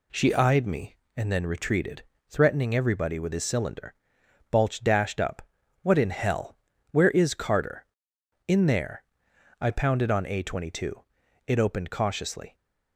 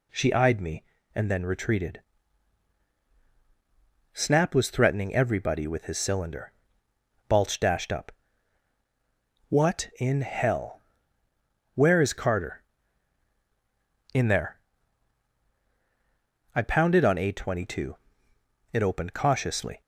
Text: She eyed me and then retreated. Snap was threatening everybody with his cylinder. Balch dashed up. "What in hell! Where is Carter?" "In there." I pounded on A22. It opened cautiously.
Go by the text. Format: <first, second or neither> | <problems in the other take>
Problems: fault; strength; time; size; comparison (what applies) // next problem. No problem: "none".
second | skips "Snap was"; at 2.1 s